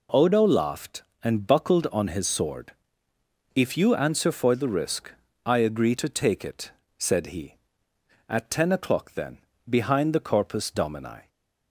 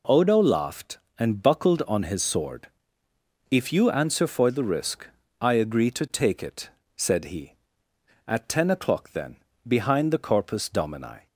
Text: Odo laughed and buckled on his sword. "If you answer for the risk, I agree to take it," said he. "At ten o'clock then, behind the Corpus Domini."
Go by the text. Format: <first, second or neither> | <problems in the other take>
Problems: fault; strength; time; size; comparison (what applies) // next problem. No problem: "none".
neither | none